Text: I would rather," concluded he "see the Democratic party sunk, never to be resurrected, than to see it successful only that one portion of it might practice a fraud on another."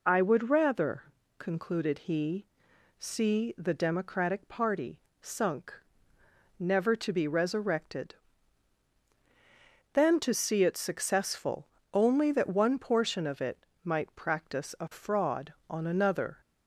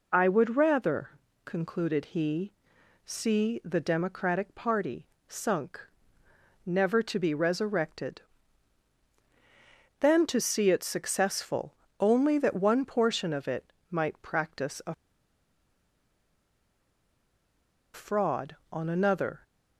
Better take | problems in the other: first | pauses between "he" and "see"; noticeable; at 2.5 s; 0.52 s long; noticeable in the first // pauses between "party" and "sunk"; slight; at 5.0 s; 0.18 s long; slight in the first // pauses between "successful" and "only"; slight; at 11.7 s; 0.24 s long; slight in the first // pauses between "it" and "might"; slight; at 13.6 s; 0.22 s long; slight in the first // pauses between "a" and "fraud"; strong; at 14.9 s; 2.9 s long

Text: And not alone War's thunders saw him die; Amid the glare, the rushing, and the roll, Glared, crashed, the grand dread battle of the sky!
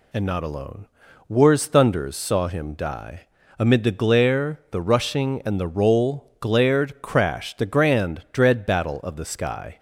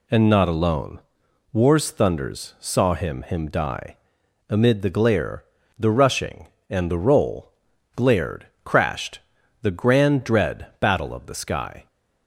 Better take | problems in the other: first | pauses between "alone" and "War's"; noticeable; at 1.0 s; 0.52 s long; also in the first // says "him" twice; at 3.2 s

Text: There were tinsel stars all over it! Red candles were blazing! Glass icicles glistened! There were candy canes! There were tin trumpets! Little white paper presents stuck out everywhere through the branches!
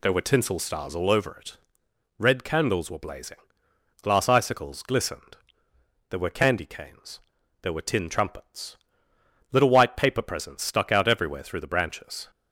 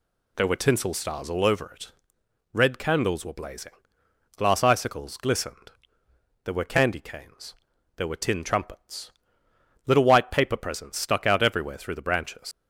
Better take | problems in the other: first | leaves "branches" unfinished; at 12.5 s; 135 ms

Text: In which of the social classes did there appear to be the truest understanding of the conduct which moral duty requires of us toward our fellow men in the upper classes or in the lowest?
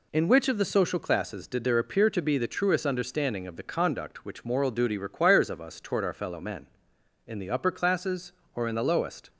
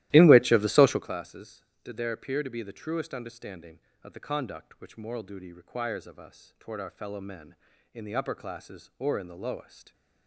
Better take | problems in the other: first | starts louder than the rest; strong; until 1.2 s; 15 dB

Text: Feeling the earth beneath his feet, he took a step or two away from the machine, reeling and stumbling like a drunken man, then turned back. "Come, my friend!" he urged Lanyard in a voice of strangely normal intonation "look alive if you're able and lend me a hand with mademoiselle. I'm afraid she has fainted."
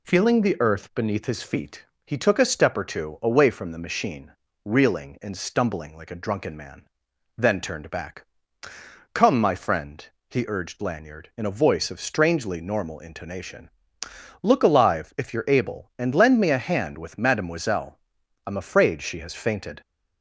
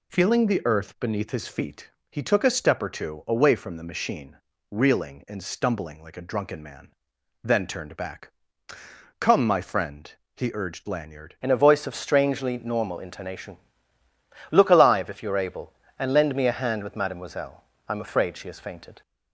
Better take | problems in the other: first | changes voice at "in"; from 11.4 s on; 7.6 s long // pauses between "intonation" and "look"; noticeable; at 13.5 s; 0.94 s long; noticeable in the first

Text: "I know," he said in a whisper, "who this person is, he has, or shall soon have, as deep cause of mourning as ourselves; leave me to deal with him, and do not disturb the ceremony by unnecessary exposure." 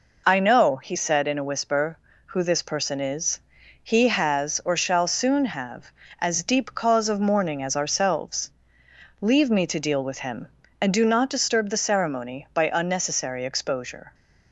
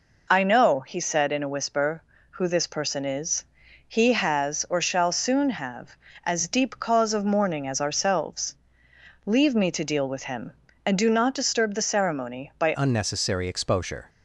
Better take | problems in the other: first | changes voice at "unnecessary"; from 12.7 s on; 1.3 s long

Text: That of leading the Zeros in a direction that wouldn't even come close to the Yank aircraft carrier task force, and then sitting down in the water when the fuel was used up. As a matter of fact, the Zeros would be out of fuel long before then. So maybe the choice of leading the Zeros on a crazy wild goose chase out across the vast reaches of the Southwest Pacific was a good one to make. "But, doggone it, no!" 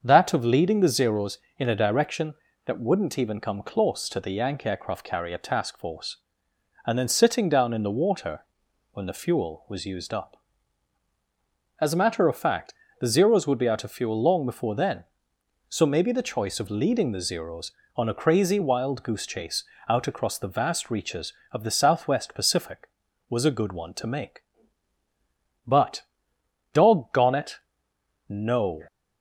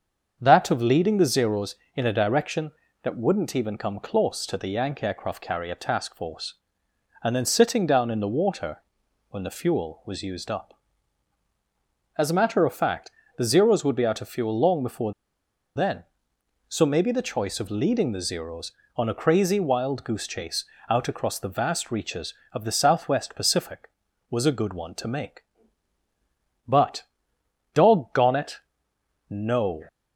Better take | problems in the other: first | starts louder than the rest; until 1.4 s; 7 dB; also in the first // pauses between "water" and "when"; noticeable; at 8.7 s; 0.52 s long; noticeable in the first // pauses between "before" and "then"; noticeable; at 15.1 s; 0.63 s long // pauses between "chase" and "out"; slight; at 20.6 s; 0.24 s long; slight in the first

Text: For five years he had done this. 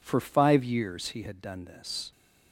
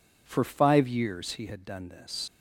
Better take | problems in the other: first | leaves "this" unfinished; at 2.2 s; 70 ms

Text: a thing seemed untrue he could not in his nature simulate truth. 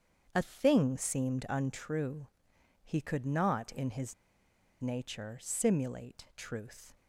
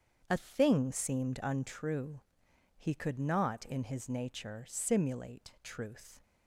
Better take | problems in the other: second | starts louder than the rest; strong; until 1.3 s; 7 dB; strong in the second // pauses between "untrue" and "he"; noticeable; at 2.2 s; 0.58 s long; noticeable in the second // pauses between "his" and "nature"; noticeable; at 4.1 s; 0.67 s long

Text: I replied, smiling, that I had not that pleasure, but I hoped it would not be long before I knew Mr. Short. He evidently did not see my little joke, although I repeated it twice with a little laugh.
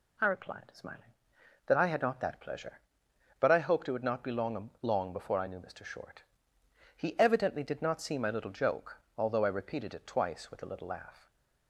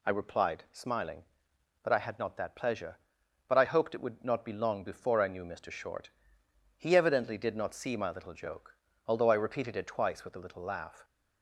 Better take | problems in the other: second | says "long" twice; at 4.8 s // stays silent after the last word; slight; from 11.1 s on; 0.5 s long

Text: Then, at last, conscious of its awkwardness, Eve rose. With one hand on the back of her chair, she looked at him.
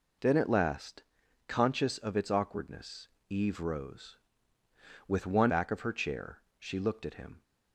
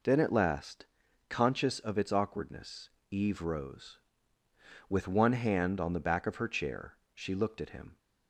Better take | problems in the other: second | skips "hand on the"; at 5.5 s

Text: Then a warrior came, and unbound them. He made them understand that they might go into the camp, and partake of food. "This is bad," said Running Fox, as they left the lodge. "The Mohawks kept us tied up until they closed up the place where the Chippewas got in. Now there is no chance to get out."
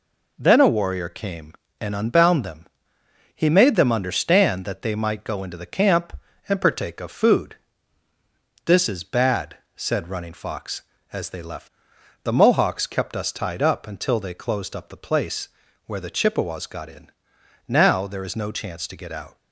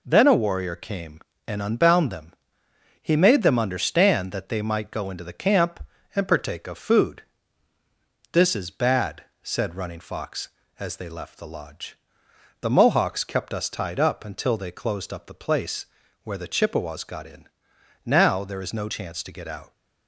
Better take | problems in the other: second | skips "the lodge"; at 11.9 s // pauses between "place" and "where"; at 15.4 s; 0.38 s long; also in the second

